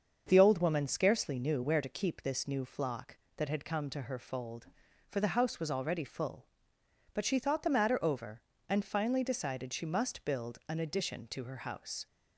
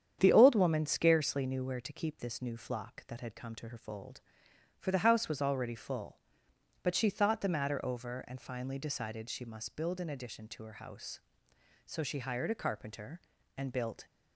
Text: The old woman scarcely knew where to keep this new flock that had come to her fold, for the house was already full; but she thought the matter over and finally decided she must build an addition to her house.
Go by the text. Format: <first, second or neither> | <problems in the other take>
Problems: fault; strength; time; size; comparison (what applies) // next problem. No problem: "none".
first | starts louder than the rest; strong; until 1.2 s; 8.5 dB; also in the first // goes on to say "So she hired a carpenter and built"; strong; from 11.8 s on; 2.2 s long